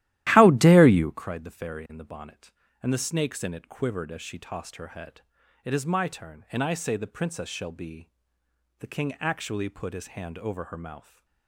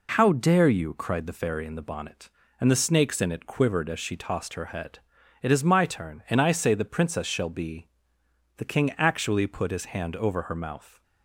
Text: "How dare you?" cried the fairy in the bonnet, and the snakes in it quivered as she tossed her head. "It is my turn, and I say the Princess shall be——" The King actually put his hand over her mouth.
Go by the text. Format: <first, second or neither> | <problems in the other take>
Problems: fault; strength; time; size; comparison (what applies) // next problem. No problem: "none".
second | starts louder than the rest; strong; until 1.2 s; 14 dB